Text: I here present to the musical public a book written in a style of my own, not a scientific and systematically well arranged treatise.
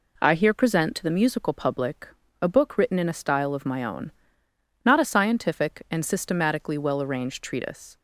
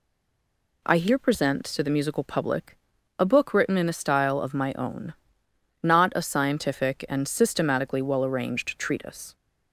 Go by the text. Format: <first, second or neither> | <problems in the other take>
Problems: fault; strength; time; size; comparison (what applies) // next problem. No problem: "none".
first | stays silent before the first word; slight; until 0.8 s; 0.8 s long // pauses between "public" and "a"; at 2.7 s; 0.40 s long; slight in the first